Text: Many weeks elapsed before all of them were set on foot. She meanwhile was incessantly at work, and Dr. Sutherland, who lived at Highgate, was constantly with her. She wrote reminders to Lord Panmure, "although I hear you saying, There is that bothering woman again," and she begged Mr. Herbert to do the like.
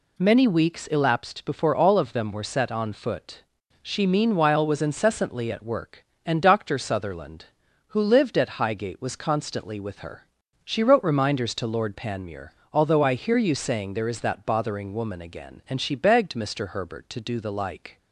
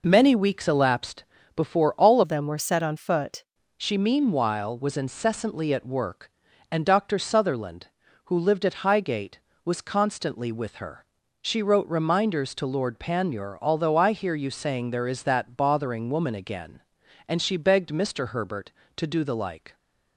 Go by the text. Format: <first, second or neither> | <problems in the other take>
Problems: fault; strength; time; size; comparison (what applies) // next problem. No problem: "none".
first | pauses between "elapsed" and "before"; slight; at 1.2 s; 0.32 s long // changes voice from "of" to "foot"; from 2.2 to 3.4 s; 1.2 s long